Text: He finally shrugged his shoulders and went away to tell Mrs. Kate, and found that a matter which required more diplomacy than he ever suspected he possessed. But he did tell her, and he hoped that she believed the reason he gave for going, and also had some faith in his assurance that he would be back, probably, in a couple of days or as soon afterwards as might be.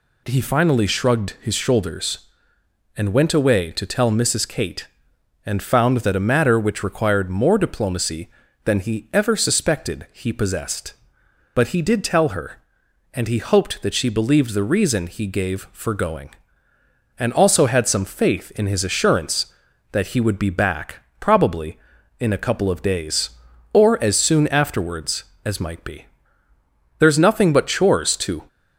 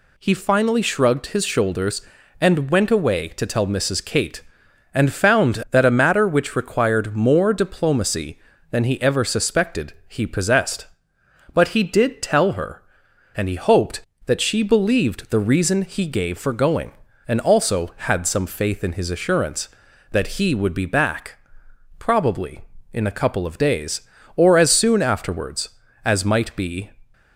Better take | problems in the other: second | goes on to say "There's nothing but chores to"; from 26.9 s on; 1.4 s long

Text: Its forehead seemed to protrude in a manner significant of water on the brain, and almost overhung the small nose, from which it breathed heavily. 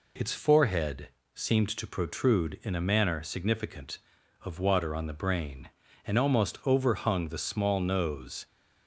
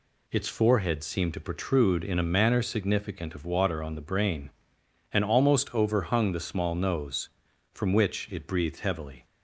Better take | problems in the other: second | pauses between "forehead" and "seemed"; slight; at 1.0 s; 0.26 s long // stops before "from which it breathed heavily"; at 8.4 s

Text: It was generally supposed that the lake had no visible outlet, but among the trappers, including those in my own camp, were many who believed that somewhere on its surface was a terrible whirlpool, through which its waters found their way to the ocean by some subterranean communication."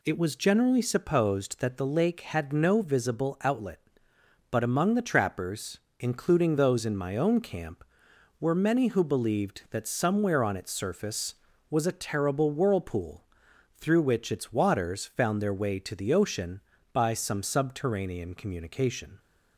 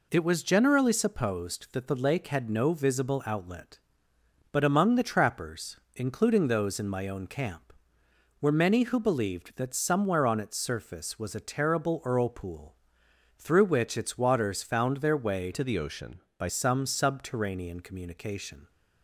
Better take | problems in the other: first | changes voice from "to" to "by"; from 15.5 to 16.4 s; 0.9 s long

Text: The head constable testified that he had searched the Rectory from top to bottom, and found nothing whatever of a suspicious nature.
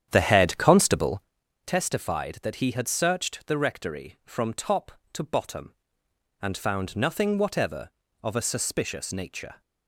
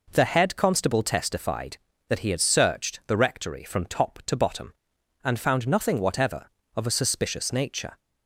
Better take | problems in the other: second | starts louder than the rest; strong; until 1.3 s; 9.5 dB // pauses between "constable" and "testified"; at 1.2 s; 0.44 s long

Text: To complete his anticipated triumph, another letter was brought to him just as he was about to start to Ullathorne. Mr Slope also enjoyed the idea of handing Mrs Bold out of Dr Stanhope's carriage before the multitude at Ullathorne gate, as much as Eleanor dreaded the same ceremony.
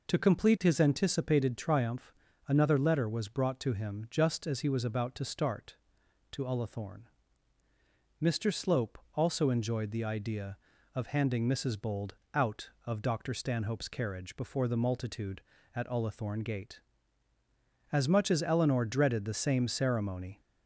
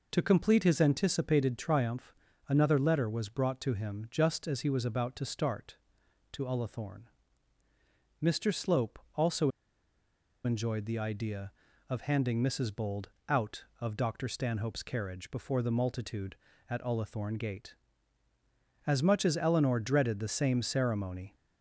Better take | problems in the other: first | pauses between "Slope" and "also"; slight; at 8.9 s; 0.18 s long; slight in the first // pauses between "also" and "enjoyed"; noticeable; at 9.5 s; 0.94 s long // pauses between "Bold" and "out"; slight; at 13.0 s; 0.20 s long; slight in the first

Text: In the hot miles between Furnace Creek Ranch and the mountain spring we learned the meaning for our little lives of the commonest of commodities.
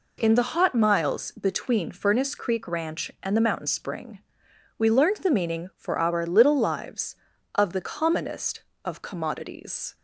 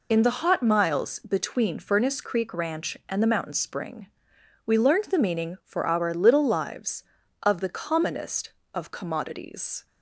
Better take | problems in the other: first | loses the start of "In"; at 0.1 s; 45 ms // pauses between "spring" and "we"; noticeable; at 4.0 s; 0.62 s long; noticeable in the first

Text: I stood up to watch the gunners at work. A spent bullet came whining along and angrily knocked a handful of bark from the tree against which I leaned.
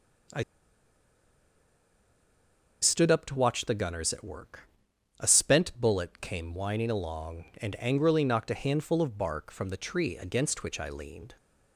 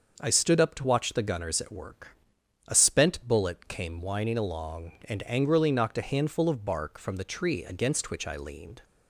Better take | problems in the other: second | starts louder than the rest; until 3.7 s; 6 dB; also in the second // pauses between "I" and "stood"; strong; at 0.4 s; 2.3 s long

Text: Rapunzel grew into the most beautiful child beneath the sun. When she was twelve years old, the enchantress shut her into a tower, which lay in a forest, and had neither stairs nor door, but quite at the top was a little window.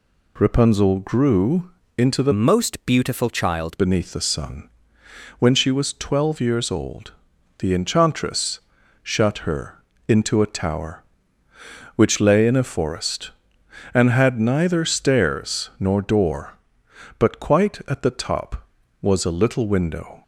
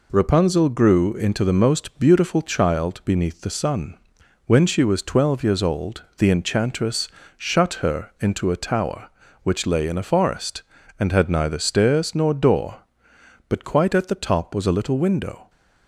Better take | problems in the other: second | pauses between "grew" and "into"; slight; at 1.7 s; 0.26 s long // changes voice from "most" to "child"; from 2.3 to 3.7 s; 1.4 s long // pauses between "enchantress" and "shut"; at 8.6 s; 0.42 s long; slight in the second // pauses between "her" and "into"; slight; at 9.8 s; 0.24 s long

